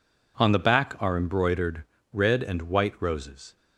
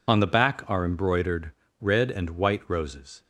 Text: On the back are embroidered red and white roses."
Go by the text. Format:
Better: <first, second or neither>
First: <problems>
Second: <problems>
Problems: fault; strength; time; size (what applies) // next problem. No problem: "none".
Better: first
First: pauses between "embroidered" and "red"; slight; at 1.8 s; 0.26 s long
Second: loses the start of "On"; at 0.0 s; 45 ms // pauses between "embroidered" and "red"; slight; at 1.5 s; 0.26 s long